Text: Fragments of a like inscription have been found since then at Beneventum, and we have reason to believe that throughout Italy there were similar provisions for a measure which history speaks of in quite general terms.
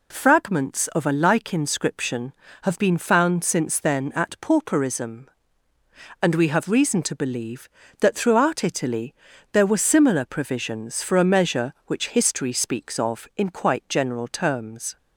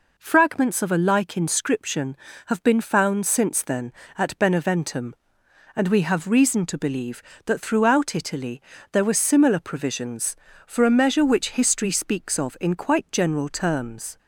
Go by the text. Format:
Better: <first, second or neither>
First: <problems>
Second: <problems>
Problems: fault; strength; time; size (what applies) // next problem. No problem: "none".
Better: second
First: says "Pauperism" for "Beneventum"; at 4.4 s // pauses between "Italy" and "there"; at 9.1 s; 0.38 s long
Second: pauses between "Italy" and "there"; slight; at 8.5 s; 0.32 s long